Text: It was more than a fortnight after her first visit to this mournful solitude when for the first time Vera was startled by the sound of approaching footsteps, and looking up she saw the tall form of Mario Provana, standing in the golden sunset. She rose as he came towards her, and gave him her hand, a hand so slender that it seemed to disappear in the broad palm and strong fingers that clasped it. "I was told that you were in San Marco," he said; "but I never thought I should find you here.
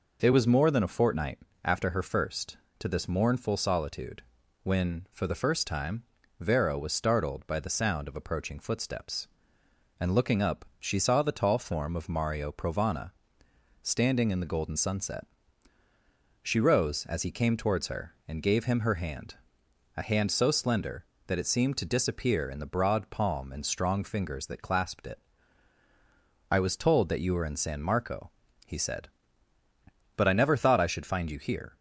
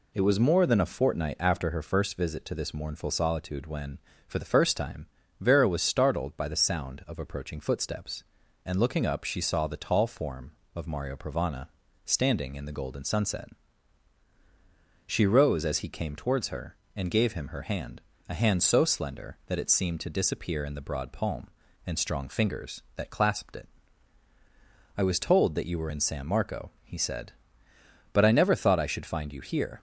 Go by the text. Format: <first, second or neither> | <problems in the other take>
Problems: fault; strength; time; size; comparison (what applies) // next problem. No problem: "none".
second | pauses between "fortnight" and "after"; slight; at 1.3 s; 0.26 s long // skips "visit"; at 2.6 s // pauses between "solitude" and "when"; at 4.2 s; 0.42 s long // pauses between "time" and "Vera"; slight; at 6.0 s; 0.36 s long; slight in the second